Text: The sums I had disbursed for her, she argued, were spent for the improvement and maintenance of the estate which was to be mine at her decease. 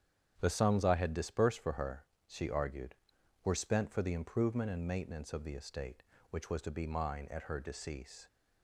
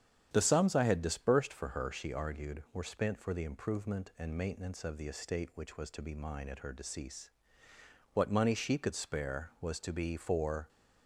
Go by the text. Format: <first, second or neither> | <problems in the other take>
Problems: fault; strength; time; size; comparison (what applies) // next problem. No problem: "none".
first | starts louder than the rest; strong; until 1.3 s; 8.5 dB; strong in the first // goes on to say "What money she could spare was to be for"; strong; from 8.1 s on; 2.5 s long